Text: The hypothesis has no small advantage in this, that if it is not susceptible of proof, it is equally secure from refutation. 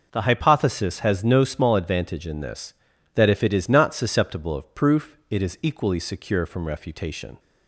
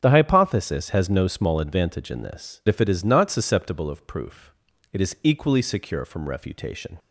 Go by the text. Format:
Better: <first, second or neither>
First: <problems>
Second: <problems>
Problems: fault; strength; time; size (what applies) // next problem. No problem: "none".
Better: first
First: none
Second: starts louder than the rest; strong; until 1.0 s; 7 dB // skips "that"; at 2.6 s